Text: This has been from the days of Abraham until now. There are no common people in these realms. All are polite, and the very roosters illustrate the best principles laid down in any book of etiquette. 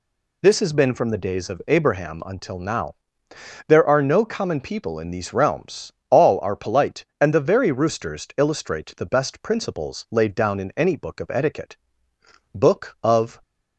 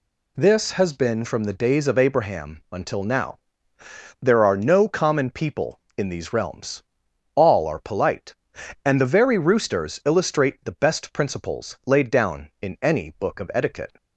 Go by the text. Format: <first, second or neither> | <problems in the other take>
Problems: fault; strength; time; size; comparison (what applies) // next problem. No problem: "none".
second | goes on to say "Book of"; noticeable; from 12.5 s on; 0.88 s long